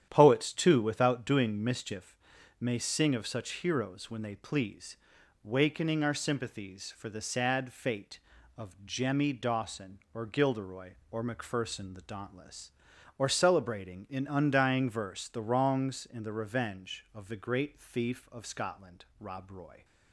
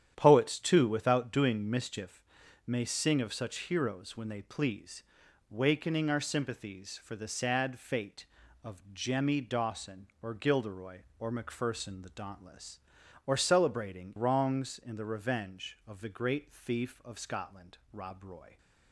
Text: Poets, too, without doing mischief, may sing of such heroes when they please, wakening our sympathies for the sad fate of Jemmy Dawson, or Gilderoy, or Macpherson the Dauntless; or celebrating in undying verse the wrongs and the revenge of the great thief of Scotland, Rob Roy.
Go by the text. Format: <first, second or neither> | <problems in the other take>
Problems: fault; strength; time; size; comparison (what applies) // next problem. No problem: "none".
first | starts louder than the rest; strong; until 1.1 s; 10 dB; strong in the first // skips "in undying verse the"; at 14.1 s